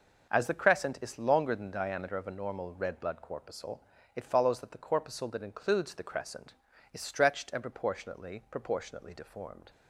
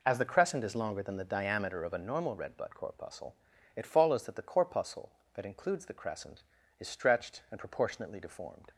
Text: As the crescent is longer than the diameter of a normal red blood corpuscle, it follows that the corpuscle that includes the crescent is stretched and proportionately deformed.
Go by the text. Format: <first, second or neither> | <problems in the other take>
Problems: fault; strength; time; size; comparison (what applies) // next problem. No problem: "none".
second | starts louder than the rest; until 1.3 s; 6 dB // says "proportionately" twice; at 8.4 s